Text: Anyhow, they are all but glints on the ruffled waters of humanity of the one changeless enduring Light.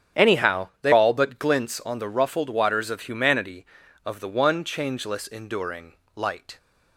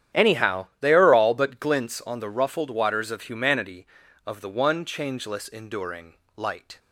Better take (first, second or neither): second